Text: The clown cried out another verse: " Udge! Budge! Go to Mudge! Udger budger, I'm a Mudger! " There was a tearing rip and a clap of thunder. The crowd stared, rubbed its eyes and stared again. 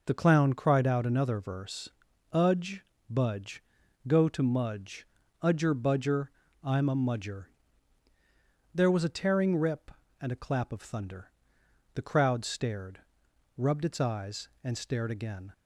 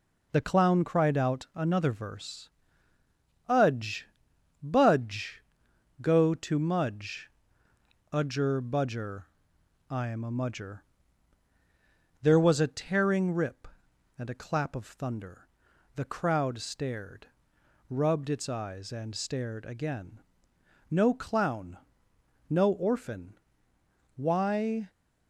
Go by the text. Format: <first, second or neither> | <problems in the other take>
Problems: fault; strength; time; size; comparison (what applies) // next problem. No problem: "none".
first | goes on to say "No clown no orphan Why"; strong; from 20.8 s on; 4.0 s long